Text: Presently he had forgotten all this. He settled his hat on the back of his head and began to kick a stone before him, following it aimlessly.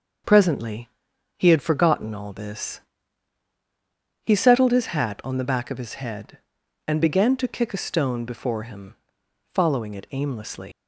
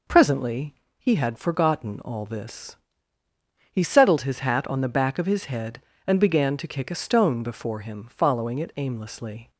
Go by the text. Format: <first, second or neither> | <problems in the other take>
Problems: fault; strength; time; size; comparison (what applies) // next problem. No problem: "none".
second | starts louder than the rest; until 1.7 s; 6.5 dB // pauses between "Presently" and "he"; noticeable; at 0.8 s; 0.48 s long; slight in the second // leaves "aimlessly" unfinished; at 10.7 s; 135 ms